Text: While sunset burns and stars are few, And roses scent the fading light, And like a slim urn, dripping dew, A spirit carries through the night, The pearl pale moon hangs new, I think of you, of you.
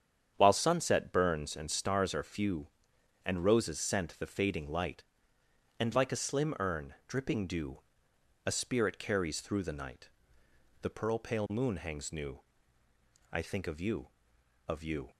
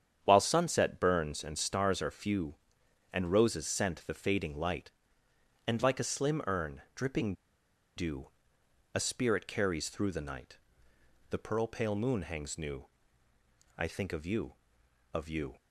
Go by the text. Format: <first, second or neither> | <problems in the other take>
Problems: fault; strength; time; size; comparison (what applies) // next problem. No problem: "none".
first | starts louder than the rest; strong; until 1.2 s; 8.5 dB; strong in the first // pauses between "dripping" and "dew"; noticeable; at 7.3 s; 0.62 s long